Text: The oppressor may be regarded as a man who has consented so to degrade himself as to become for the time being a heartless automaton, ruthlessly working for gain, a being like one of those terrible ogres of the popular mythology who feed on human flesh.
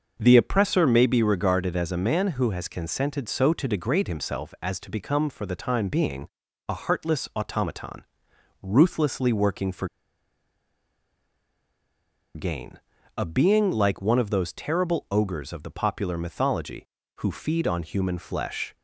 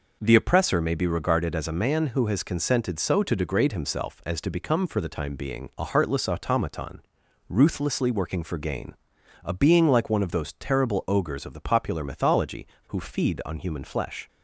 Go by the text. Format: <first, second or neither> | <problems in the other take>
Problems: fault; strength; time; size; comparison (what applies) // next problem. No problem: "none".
second | starts louder than the rest; until 1.2 s; 6.5 dB // pauses between "being" and "a"; at 6.2 s; 0.40 s long // pauses between "for" and "gain"; strong; at 9.8 s; 2.4 s long